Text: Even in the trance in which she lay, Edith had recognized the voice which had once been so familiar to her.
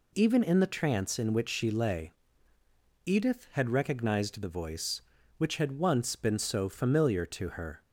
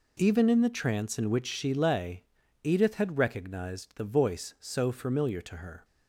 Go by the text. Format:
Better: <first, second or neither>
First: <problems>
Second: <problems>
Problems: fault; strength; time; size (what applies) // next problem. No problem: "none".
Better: first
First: none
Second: skips "which had once been"; at 4.5 s